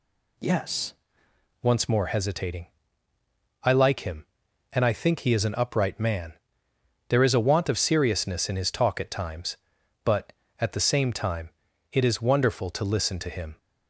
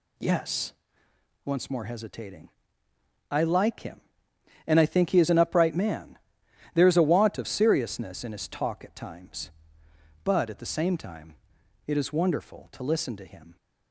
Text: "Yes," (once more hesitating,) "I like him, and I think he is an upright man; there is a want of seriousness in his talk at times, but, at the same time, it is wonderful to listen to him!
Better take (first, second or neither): second